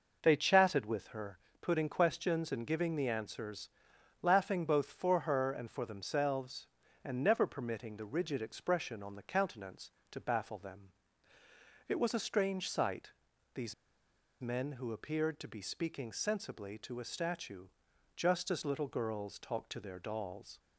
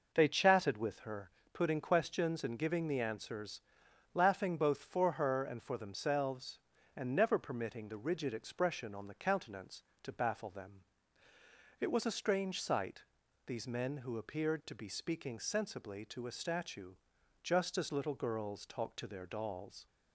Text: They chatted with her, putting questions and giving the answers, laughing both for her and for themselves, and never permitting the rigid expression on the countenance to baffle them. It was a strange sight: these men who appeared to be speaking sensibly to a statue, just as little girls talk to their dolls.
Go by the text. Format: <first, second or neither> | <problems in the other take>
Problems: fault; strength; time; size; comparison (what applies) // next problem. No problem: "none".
second | pauses between "these" and "men"; noticeable; at 13.7 s; 0.68 s long